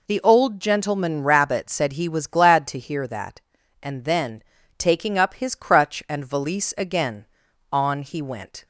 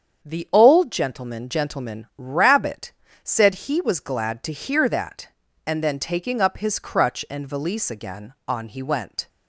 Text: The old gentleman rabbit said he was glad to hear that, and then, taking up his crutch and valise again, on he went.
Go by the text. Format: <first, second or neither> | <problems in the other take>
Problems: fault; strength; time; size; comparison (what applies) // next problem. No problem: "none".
first | starts louder than the rest; strong; until 1.3 s; 7.5 dB // says "gentleman" twice; at 1.4 s // pauses between "rabbit" and "said"; slight; at 2.9 s; 0.32 s long